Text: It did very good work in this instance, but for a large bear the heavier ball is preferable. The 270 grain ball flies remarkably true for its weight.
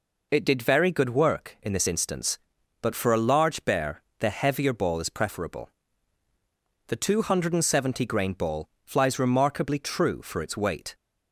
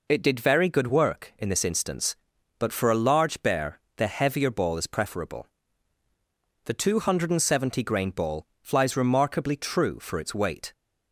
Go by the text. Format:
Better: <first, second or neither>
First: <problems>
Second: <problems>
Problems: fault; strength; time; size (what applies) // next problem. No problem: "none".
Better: neither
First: pauses between "bear" and "the"; slight; at 4.0 s; 0.20 s long // pauses between "ball" and "flies"; slight; at 8.6 s; 0.16 s long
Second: pauses between "bear" and "the"; slight; at 3.7 s; 0.20 s long // pauses between "ball" and "flies"; slight; at 8.4 s; 0.16 s long